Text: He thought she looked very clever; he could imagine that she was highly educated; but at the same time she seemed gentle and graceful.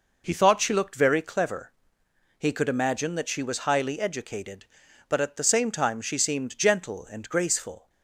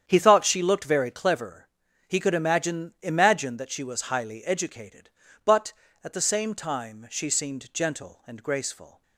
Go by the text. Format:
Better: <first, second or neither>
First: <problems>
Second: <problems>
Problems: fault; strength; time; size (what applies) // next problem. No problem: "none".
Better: first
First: none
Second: starts louder than the rest; strong; until 1.0 s; 8.5 dB // says "imagine" twice; at 3.0 s